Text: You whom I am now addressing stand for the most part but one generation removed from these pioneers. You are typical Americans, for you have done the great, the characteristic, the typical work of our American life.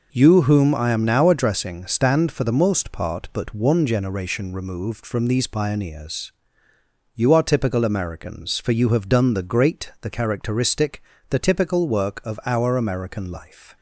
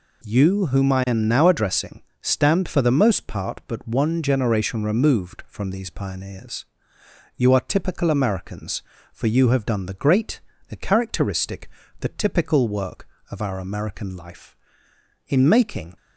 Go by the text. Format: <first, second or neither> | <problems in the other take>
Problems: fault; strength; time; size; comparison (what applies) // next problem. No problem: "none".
first | pauses between "addressing" and "stand"; slight; at 2.0 s; 0.22 s long // goes on to say "In making"; noticeable; from 15.2 s on; 0.68 s long